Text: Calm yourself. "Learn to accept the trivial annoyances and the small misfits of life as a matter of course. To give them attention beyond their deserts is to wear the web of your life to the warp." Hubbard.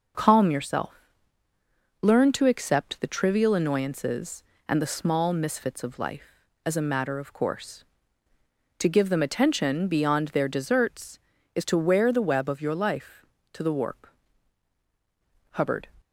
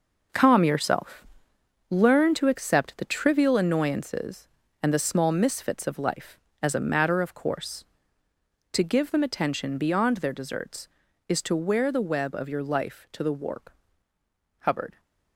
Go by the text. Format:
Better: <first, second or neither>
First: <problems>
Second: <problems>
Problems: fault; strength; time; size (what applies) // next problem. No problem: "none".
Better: first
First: none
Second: gets quieter; strong; throughout; 9 dB